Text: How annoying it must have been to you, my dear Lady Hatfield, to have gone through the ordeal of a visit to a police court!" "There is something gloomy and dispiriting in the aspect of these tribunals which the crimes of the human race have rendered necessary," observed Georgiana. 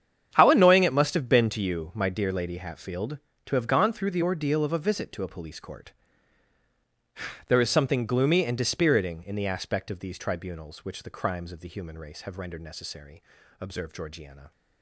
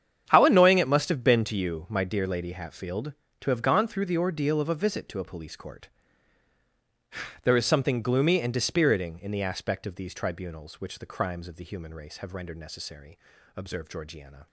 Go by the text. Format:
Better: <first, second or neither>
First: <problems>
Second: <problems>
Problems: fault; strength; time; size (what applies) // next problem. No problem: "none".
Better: neither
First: starts louder than the rest; strong; until 1.3 s; 9 dB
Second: starts louder than the rest; strong; until 1.3 s; 9 dB